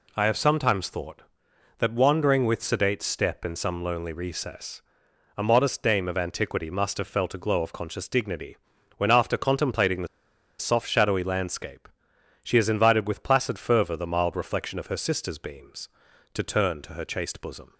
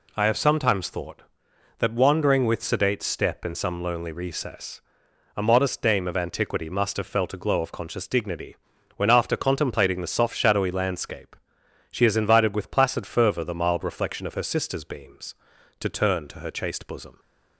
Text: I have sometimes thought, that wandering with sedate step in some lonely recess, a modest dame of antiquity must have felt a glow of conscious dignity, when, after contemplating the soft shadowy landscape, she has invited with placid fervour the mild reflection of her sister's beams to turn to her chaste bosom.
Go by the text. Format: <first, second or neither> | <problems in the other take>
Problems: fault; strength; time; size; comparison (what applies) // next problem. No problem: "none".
second | pauses between "the" and "soft"; noticeable; at 10.0 s; 0.51 s long